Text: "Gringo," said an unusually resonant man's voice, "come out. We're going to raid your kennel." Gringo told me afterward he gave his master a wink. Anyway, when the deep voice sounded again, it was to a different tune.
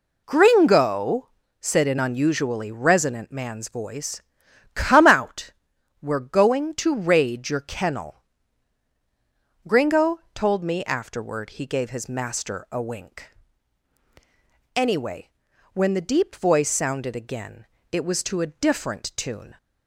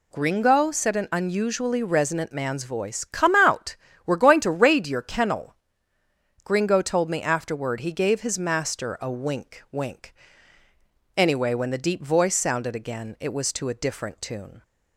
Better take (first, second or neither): first